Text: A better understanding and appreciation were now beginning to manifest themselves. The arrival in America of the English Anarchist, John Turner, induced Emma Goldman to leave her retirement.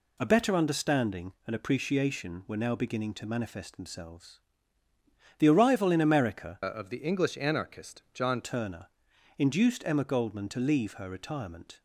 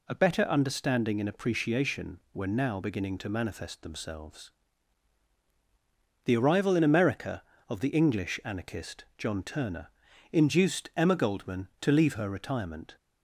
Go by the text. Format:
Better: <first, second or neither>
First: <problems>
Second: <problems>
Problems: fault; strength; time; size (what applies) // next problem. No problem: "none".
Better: second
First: changes voice from "of" to "John"; from 6.6 to 8.4 s; 1.8 s long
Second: none